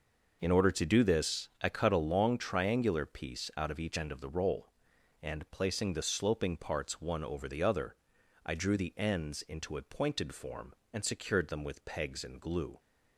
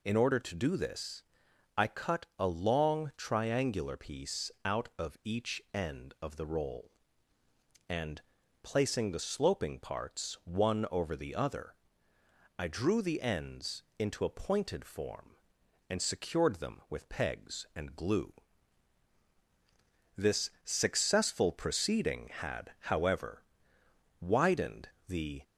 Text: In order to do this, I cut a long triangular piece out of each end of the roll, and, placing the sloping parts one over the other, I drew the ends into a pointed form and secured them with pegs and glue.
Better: first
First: none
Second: pauses between "ends" and "into"; slight; at 13.8 s; 0.16 s long // goes on to say "This successful proceeding had however widened the"; strong; from 20.1 s on; 5.2 s long

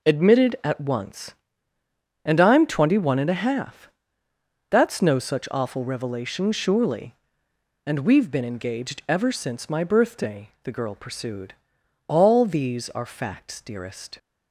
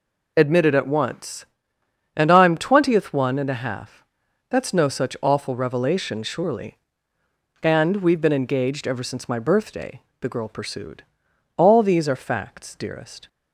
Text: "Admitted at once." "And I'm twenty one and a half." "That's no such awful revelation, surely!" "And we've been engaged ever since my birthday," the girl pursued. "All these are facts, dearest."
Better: first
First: none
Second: says "twentieth" for "twenty"; at 2.5 s

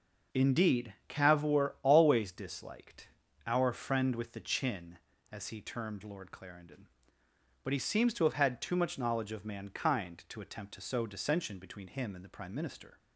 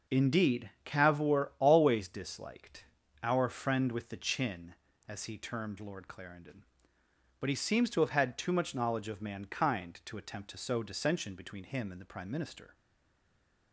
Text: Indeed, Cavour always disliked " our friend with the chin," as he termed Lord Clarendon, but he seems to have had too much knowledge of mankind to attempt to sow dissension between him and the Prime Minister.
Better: first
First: starts louder than the rest; until 1.4 s; 6.5 dB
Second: starts louder than the rest; until 1.2 s; 6 dB // stays silent after the last word; from 12.7 s on; 1.0 s long

